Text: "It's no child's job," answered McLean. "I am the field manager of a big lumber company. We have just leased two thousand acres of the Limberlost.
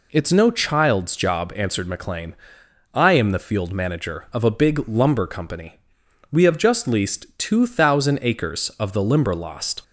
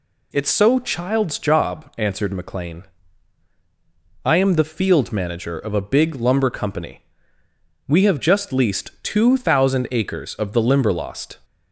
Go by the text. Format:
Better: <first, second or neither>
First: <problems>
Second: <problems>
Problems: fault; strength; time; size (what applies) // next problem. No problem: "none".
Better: first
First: none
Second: says "so" for "no"; at 0.4 s